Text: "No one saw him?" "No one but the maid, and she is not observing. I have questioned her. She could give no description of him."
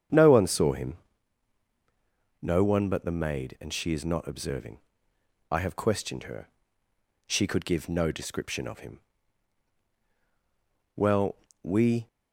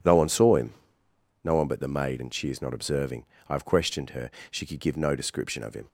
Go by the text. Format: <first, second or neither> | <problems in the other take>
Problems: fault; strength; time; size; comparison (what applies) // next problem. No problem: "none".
second | starts louder than the rest; strong; until 2.5 s; 8 dB // goes on to say "Well we"; noticeable; from 10.9 s on; 1.1 s long